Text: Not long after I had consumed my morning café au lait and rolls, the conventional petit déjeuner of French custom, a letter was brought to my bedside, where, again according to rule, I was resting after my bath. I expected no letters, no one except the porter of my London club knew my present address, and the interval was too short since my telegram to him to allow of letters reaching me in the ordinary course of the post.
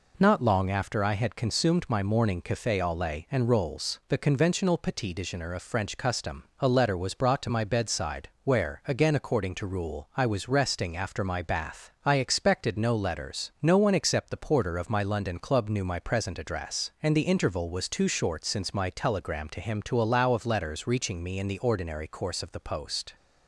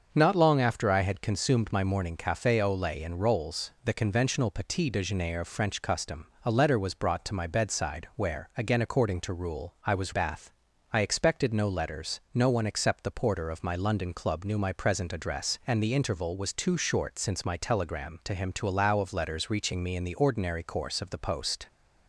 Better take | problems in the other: first | starts louder than the rest; until 1.1 s; 6.5 dB // skips "resting after my"; at 10.1 s

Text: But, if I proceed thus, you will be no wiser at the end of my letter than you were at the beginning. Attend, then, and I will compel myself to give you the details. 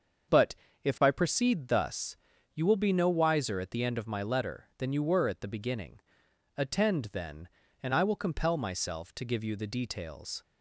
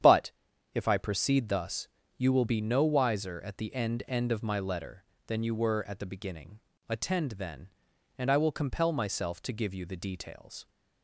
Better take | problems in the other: first | starts louder than the rest; strong; until 1.4 s; 9 dB; also in the first // says "end" twice; at 4.0 s

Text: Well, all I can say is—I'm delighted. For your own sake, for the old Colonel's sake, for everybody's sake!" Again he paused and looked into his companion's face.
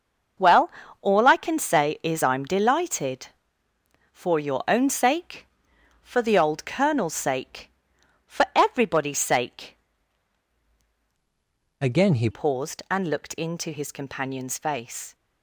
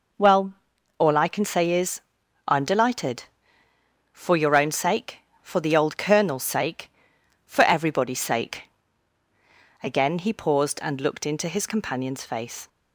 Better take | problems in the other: second | starts louder than the rest; until 1.6 s; 6 dB // changes voice from "Again" to "he"; from 11.8 to 12.2 s; 0.4 s long

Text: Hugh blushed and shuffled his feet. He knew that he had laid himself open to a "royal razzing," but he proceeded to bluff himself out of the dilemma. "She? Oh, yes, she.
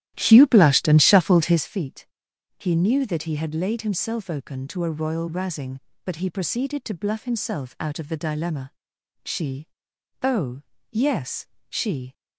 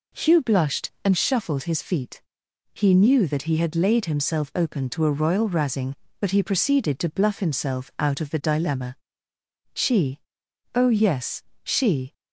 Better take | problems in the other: second | starts louder than the rest; strong; until 1.6 s; 13 dB

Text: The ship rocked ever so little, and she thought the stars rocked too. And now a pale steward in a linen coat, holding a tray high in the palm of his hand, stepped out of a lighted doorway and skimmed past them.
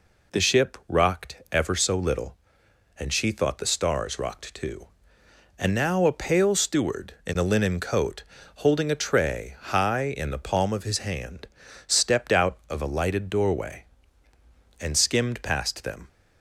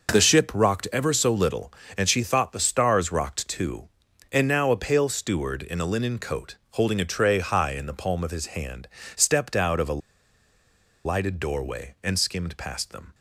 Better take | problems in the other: first | pauses between "a" and "lighted"; at 9.9 s; 1.0 s long

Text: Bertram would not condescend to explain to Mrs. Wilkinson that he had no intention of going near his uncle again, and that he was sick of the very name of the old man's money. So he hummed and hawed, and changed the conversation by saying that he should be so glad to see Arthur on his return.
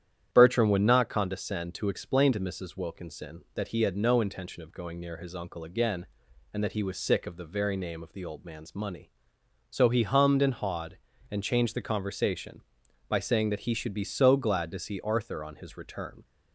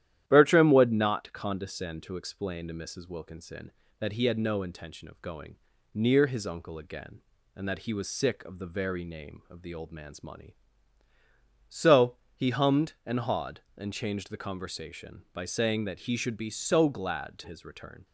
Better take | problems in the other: first | starts louder than the rest; strong; until 1.2 s; 12 dB; strong in the first // pauses between "going" and "near"; at 5.5 s; 0.38 s long // pauses between "So" and "he"; slight; at 12.1 s; 0.18 s long // skips "see Arthur on"; at 17.4 s

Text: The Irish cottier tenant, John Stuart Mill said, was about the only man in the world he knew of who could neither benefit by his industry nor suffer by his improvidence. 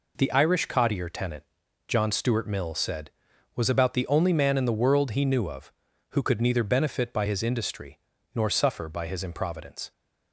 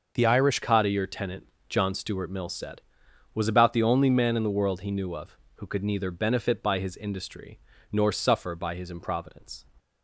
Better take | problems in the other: first | starts louder than the rest; until 1.2 s; 6 dB // changes voice at "cottier"; from 0.6 s on; 9.0 s long // pauses between "industry" and "nor"; slight; at 7.5 s; 0.34 s long; slight in the first

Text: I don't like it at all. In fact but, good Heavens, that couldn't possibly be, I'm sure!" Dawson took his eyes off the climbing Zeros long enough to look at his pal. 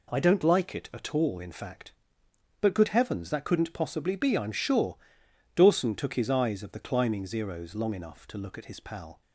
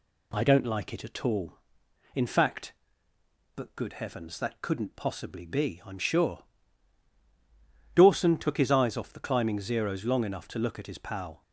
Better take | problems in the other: second | says "of" for "off"; at 6.6 s

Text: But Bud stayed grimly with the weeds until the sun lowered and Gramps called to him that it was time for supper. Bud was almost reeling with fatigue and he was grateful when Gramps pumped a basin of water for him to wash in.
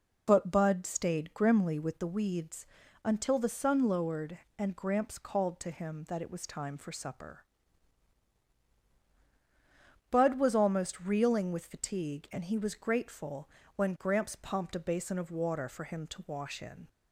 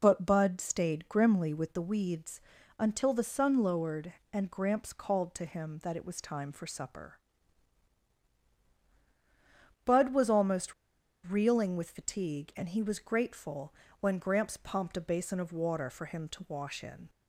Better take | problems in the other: first | pauses between "weeds" and "until"; slight; at 2.4 s; 0.36 s long; slight in the first // pauses between "almost" and "reeling"; noticeable; at 10.7 s; 0.51 s long // pauses between "grateful" and "when"; slight; at 13.7 s; 0.26 s long; slight in the first

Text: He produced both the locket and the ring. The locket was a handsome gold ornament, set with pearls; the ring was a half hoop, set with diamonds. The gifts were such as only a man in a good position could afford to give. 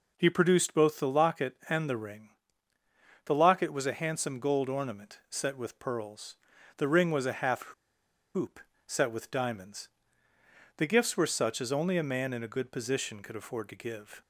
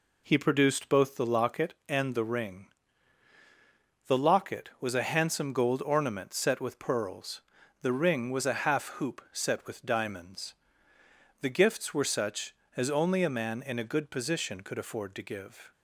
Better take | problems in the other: second | pauses between "half" and "hoop"; noticeable; at 7.6 s; 0.71 s long

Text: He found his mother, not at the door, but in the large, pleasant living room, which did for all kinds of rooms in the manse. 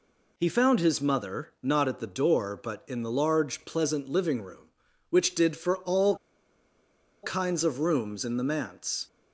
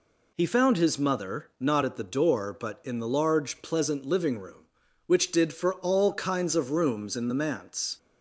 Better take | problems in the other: second | pauses between "all" and "kinds"; at 6.1 s; 1.0 s long

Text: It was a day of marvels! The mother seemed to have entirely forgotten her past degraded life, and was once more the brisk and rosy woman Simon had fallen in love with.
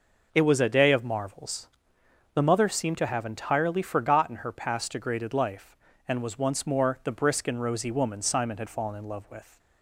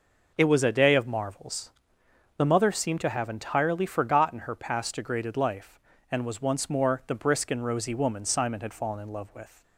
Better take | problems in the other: neither | none

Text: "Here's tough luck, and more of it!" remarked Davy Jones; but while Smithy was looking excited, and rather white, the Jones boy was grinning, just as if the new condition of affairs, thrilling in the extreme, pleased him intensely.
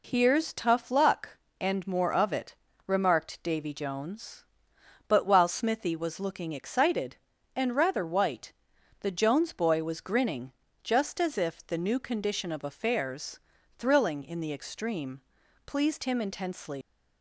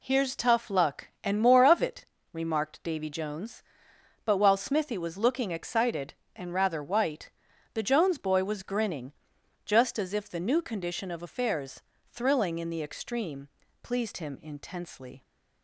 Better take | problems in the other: second | leaves "intensely" unfinished; at 16.8 s; 100 ms

